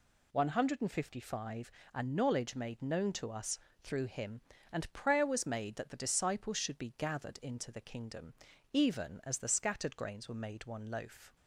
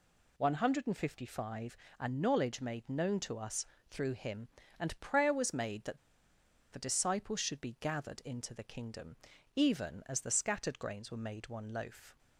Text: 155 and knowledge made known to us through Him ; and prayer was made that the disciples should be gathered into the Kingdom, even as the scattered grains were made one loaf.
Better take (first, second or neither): first